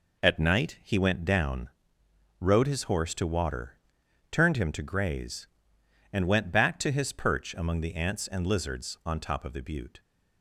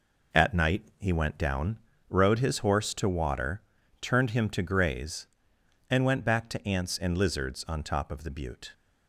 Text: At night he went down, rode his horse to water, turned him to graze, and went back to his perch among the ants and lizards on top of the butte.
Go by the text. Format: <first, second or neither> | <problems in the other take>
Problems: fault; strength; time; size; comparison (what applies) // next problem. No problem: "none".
first | skips "his perch among the"; at 6.6 s